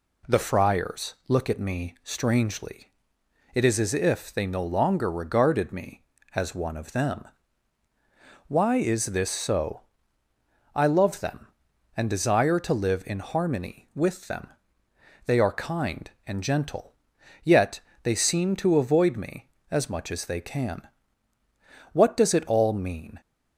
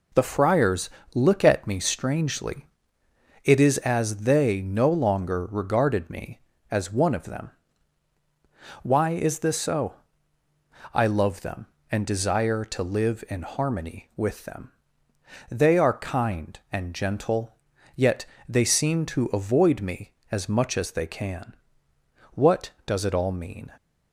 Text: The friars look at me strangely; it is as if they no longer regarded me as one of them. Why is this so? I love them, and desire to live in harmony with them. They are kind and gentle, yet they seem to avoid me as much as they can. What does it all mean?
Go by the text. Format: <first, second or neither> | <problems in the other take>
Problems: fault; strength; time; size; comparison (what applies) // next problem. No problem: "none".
first | pauses between "friars" and "look"; slight; at 0.8 s; 0.24 s long // skips "if"; at 4.1 s // pauses between "yet" and "they"; slight; at 18.2 s; 0.20 s long; slight in the first